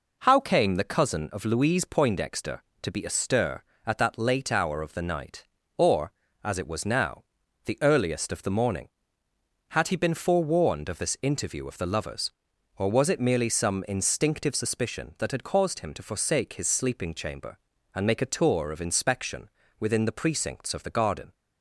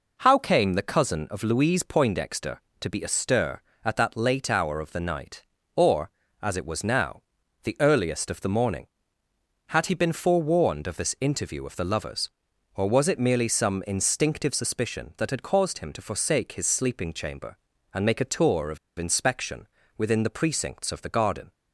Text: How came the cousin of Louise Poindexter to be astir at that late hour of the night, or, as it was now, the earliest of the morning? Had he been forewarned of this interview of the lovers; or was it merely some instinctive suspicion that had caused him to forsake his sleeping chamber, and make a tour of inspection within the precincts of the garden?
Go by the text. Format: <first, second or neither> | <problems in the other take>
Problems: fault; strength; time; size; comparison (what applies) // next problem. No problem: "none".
first | pauses between "of" and "inspection"; slight; at 18.7 s; 0.21 s long // pauses between "inspection" and "within"; slight; at 19.6 s; 0.28 s long; slight in the first